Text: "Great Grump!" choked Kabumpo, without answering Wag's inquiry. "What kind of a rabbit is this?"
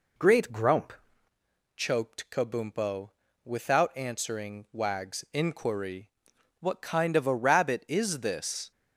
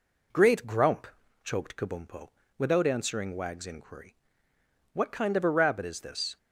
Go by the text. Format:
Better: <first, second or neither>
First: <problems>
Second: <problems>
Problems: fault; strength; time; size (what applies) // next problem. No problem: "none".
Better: second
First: changes voice at "choked"; from 1.7 s on; 7.0 s long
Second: none